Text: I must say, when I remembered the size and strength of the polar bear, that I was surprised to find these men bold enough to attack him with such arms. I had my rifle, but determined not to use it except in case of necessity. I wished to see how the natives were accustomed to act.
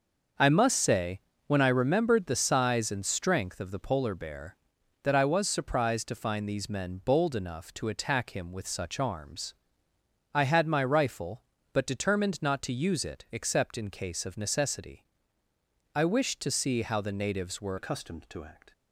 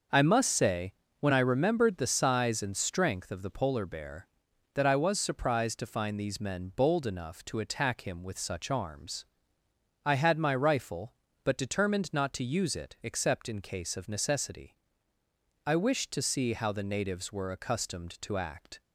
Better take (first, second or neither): second